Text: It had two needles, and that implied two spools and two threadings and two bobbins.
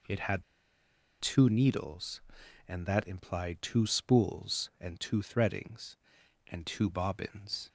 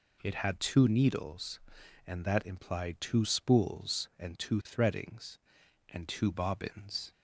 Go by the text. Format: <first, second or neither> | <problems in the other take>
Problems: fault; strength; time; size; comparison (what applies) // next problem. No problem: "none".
second | pauses between "had" and "two"; noticeable; at 0.4 s; 0.76 s long